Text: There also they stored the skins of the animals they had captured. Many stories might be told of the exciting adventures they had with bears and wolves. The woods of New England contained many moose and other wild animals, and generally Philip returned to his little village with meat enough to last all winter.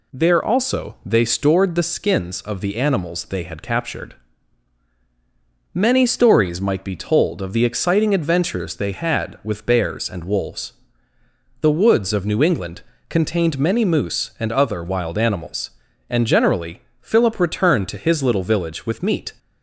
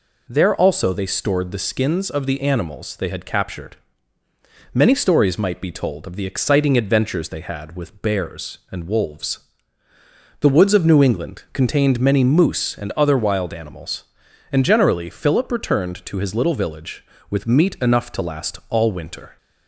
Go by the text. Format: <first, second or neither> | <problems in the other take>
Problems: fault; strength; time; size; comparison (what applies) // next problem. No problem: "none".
second | pauses between "England" and "contained"; slight; at 12.8 s; 0.26 s long // pauses between "generally" and "Philip"; slight; at 16.8 s; 0.18 s long // stops before "enough to last all winter"; at 19.3 s